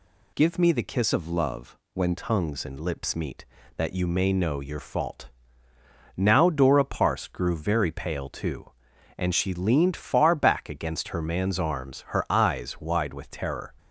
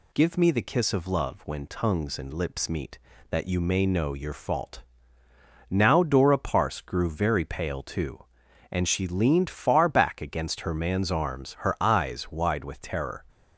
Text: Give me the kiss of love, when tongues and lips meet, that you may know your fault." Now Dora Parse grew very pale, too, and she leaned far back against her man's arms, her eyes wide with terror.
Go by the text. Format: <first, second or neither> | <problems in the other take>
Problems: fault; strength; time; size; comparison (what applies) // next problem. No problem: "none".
second | changes voice from "of" to "when"; from 1.1 to 2.1 s; 1.0 s long